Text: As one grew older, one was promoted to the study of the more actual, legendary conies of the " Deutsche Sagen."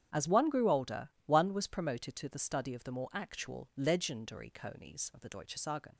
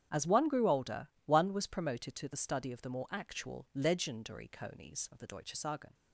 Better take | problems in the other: neither | starts louder than the rest; strong; the same in both

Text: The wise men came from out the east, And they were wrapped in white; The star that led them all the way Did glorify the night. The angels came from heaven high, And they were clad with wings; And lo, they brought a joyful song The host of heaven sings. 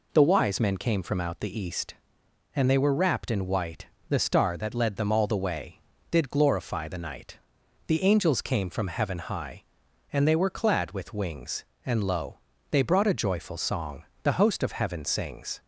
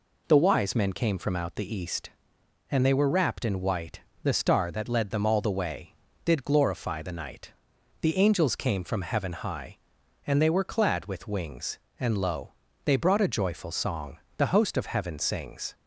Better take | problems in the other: neither | pauses between "song" and "The"; slight; the same in both

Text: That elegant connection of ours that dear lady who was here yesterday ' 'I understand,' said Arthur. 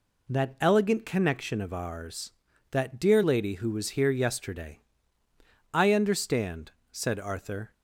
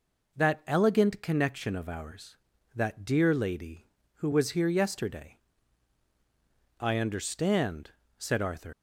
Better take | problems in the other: first | leaves "Arthur" unfinished; at 8.7 s; 100 ms

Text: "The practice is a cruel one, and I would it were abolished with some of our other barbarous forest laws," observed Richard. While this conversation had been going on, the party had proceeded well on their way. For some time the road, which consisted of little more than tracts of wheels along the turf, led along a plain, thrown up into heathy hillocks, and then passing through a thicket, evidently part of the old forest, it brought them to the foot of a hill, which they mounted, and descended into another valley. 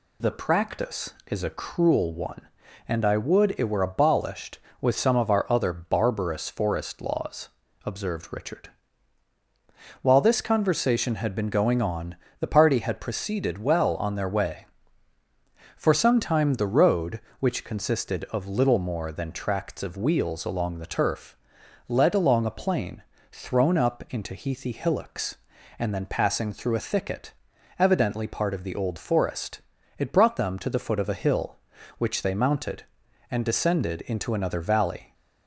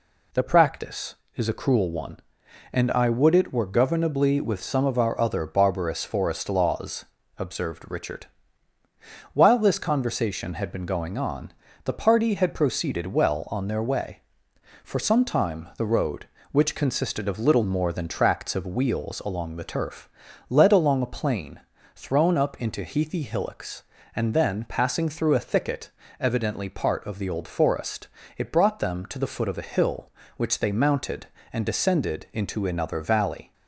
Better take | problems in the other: first | says "governably" for "abolished"; at 3.6 s

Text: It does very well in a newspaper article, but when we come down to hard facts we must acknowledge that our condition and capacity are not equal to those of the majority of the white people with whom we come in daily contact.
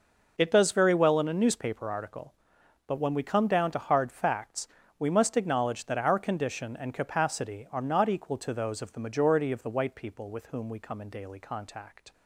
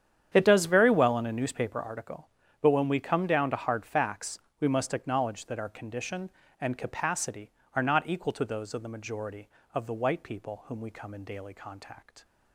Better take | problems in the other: first | starts louder than the rest; strong; until 1.3 s; 9 dB // pauses between "facts" and "we"; slight; at 4.3 s; 0.22 s long; slight in the first // skips "with"; at 10.6 s

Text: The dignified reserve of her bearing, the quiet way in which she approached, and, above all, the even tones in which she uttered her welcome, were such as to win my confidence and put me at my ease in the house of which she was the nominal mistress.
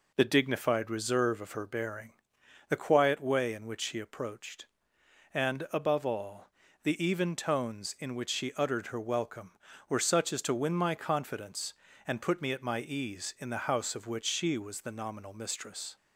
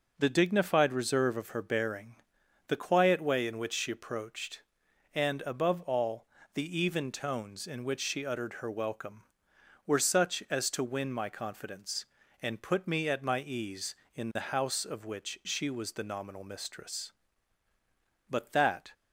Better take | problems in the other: first | goes on to say "But that"; noticeable; from 18.2 s on; 0.64 s long

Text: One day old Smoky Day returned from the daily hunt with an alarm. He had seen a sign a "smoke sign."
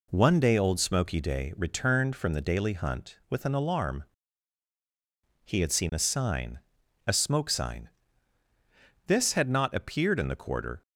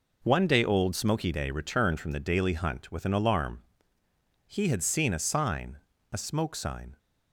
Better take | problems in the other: second | pauses between "sign" and "a"; noticeable; at 6.5 s; 0.48 s long; slight in the second // goes on to say "This had not appeared in the quarter"; strong; from 9.0 s on; 1.7 s long

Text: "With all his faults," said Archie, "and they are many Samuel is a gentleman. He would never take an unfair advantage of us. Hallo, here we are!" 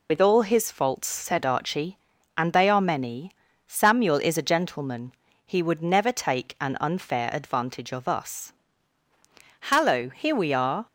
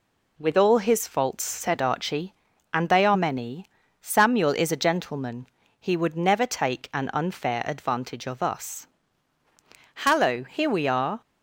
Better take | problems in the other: second | loses the start of "With"; at 0.0 s; 80 ms // pauses between "many" and "Samuel"; slight; at 3.3 s; 0.34 s long; slight in the second

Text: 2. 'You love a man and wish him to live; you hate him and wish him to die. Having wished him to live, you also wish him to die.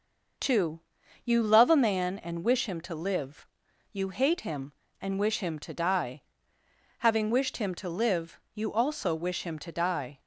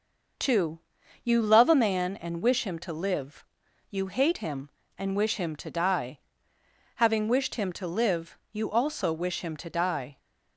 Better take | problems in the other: neither | none

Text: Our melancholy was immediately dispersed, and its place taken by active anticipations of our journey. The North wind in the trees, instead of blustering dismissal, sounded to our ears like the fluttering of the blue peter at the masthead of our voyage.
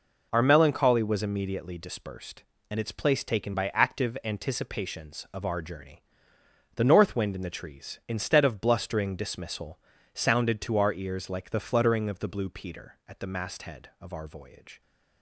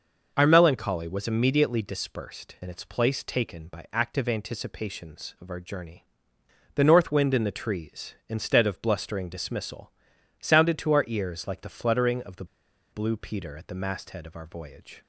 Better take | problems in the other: first | pauses between "the" and "blue"; noticeable; at 12.4 s; 0.47 s long

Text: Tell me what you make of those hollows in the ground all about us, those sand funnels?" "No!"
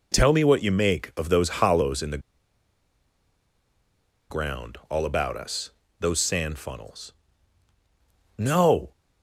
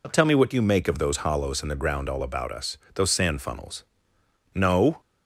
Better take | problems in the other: second | pauses between "the" and "ground"; strong; at 2.1 s; 2.1 s long

